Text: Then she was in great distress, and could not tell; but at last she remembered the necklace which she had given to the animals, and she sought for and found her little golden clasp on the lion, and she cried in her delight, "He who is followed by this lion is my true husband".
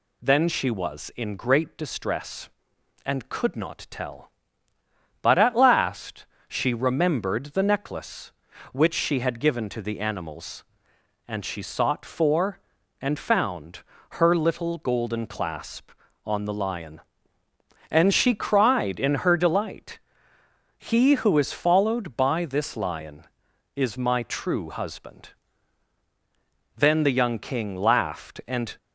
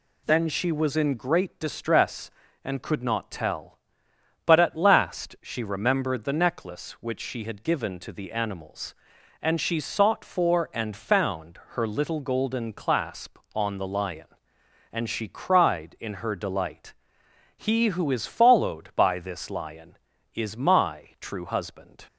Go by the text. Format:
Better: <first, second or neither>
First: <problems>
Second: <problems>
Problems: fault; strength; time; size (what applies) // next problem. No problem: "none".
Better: second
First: pauses between "last" and "she"; slight; at 6.2 s; 0.22 s long // pauses between "found" and "her"; slight; at 13.8 s; 0.30 s long // goes on to say "Then the young King laughed and"; strong; from 26.7 s on; 2.0 s long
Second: none